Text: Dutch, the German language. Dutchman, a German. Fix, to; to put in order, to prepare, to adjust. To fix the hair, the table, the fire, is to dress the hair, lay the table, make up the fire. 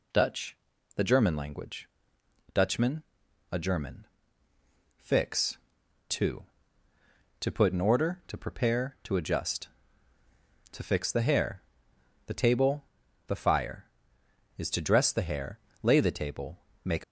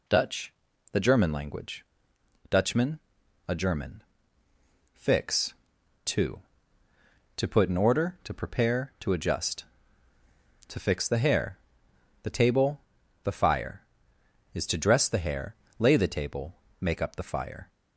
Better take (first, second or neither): second